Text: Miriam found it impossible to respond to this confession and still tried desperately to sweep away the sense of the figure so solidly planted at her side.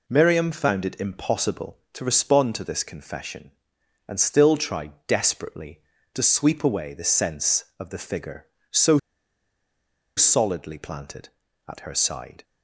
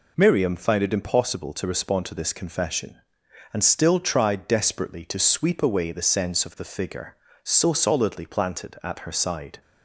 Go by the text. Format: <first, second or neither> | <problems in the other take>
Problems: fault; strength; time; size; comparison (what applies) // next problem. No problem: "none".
second | pauses between "tried" and "desperately"; slight; at 4.9 s; 0.16 s long // pauses between "so" and "solidly"; at 8.9 s; 1.1 s long